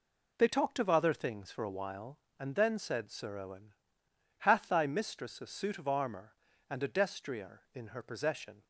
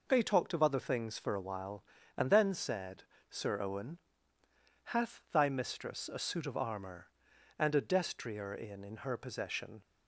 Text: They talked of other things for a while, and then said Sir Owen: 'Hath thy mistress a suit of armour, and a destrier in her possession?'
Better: first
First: none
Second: pauses between "said" and "Sir"; slight; at 3.0 s; 0.26 s long // says "in" twice; at 8.8 s

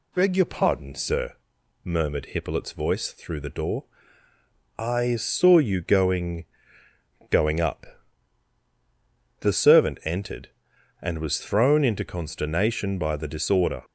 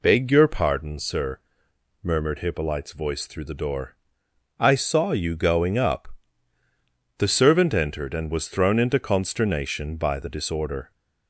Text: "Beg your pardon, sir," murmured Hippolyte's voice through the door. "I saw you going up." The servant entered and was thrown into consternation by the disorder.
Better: second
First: says "going" twice; at 7.3 s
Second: none

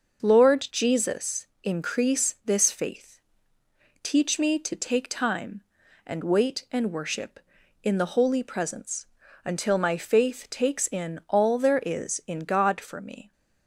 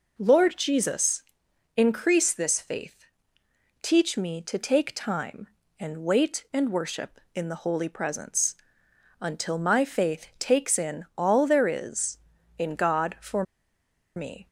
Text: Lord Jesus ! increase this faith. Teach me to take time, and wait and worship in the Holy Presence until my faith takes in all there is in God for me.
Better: first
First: pauses between "Presence" and "until"; at 9.0 s; 0.38 s long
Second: pauses between "Presence" and "until"; noticeable; at 8.5 s; 0.66 s long // pauses between "for" and "me"; noticeable; at 13.4 s; 0.73 s long

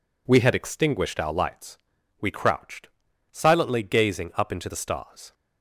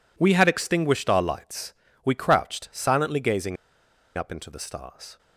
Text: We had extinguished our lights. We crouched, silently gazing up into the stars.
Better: first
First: none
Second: pauses between "gazing" and "up"; noticeable; at 3.5 s; 0.62 s long

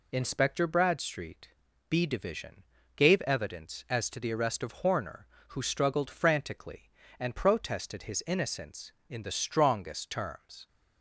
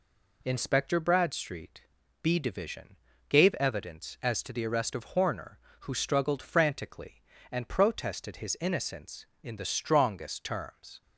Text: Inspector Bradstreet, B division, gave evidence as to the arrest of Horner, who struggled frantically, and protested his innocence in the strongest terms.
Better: second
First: loses the start of "Inspector"; at 0.1 s; 40 ms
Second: none

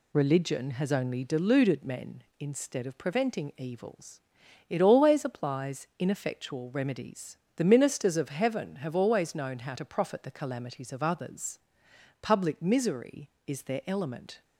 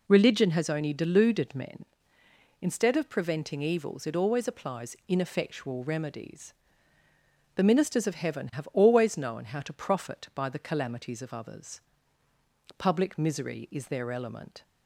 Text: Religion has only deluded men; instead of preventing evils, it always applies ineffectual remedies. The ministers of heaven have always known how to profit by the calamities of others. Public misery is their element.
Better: second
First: skips "by"; at 10.2 s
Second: none

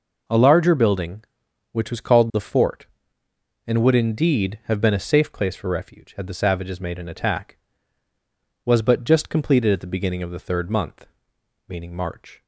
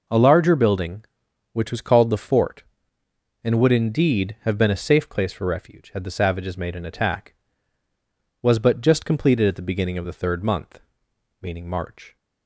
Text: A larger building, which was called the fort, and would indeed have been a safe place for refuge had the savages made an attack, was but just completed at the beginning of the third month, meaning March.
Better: neither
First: none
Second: none

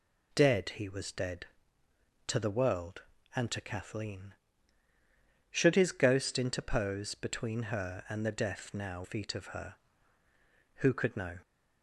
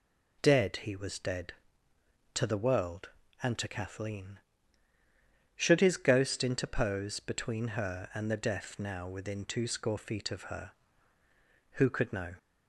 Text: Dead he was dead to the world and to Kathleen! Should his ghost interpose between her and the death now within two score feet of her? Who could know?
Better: second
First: skips "within two score"; at 9.0 s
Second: none

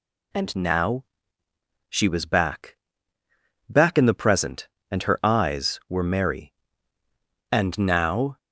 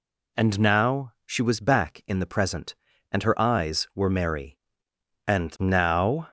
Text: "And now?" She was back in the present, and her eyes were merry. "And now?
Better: second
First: says "back" twice; at 3.7 s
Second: none

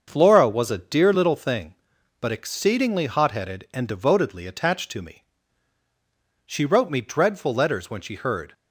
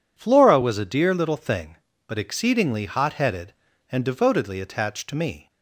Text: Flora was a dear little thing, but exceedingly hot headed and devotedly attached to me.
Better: second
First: starts louder than the rest; until 1.0 s; 6.5 dB // goes on to say "She wrote me dreadful letters when she heard"; strong; from 6.4 s on; 2.0 s long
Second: none

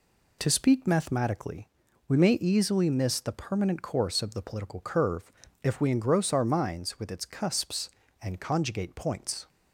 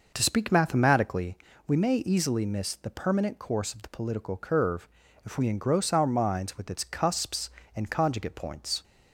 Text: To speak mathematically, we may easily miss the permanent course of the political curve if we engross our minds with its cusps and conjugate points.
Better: first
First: pauses between "curve" and "if"; slight; at 5.3 s; 0.32 s long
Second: starts louder than the rest; noticeable; until 1.2 s; 5.5 dB // pauses between "curve" and "if"; slight; at 4.8 s; 0.36 s long

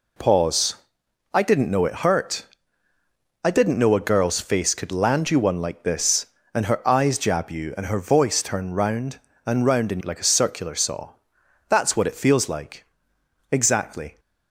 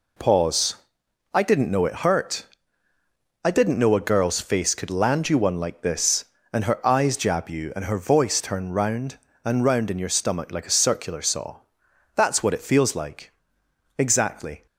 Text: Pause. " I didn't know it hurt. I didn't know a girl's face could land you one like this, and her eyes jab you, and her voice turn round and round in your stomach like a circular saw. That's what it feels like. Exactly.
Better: second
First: skips "your stomach"; at 10.0 s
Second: none

